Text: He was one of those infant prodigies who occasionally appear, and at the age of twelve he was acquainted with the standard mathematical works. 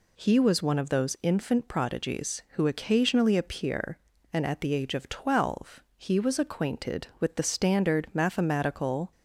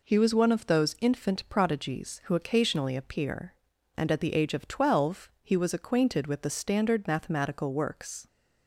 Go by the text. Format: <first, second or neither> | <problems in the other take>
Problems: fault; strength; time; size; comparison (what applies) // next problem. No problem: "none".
second | pauses between "twelve" and "he"; slight; at 5.8 s; 0.16 s long // stops before "works"; at 9.1 s